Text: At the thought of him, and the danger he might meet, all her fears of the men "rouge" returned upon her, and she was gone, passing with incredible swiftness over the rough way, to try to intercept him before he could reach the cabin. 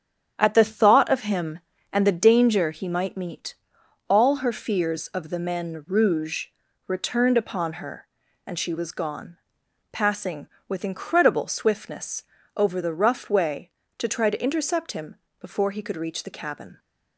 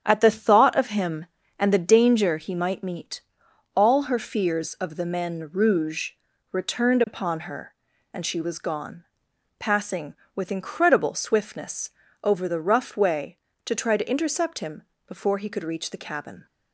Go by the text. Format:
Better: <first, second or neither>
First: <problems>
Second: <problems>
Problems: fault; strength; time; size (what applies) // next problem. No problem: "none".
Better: neither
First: starts louder than the rest; strong; until 1.3 s; 9 dB // pauses between "rouge" and "returned"; at 6.4 s; 0.40 s long // pauses between "swiftness" and "over"; slight; at 12.2 s; 0.32 s long // pauses between "him" and "before"; slight; at 15.1 s; 0.24 s long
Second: starts louder than the rest; strong; until 1.0 s; 9 dB // pauses between "rouge" and "returned"; at 6.1 s; 0.40 s long // pauses between "swiftness" and "over"; slight; at 11.8 s; 0.32 s long // pauses between "him" and "before"; slight; at 14.8 s; 0.24 s long